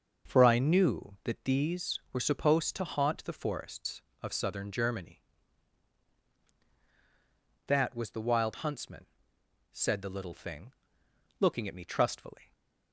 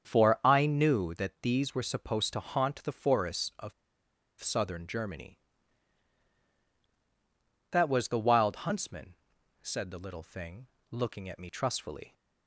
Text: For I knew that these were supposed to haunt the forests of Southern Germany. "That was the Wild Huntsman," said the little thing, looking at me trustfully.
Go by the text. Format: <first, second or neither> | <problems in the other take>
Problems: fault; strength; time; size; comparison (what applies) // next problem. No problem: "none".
first | starts louder than the rest; strong; until 1.1 s; 7.5 dB; noticeable in the first // pauses between "of" and "Southern"; noticeable; at 3.7 s; 0.68 s long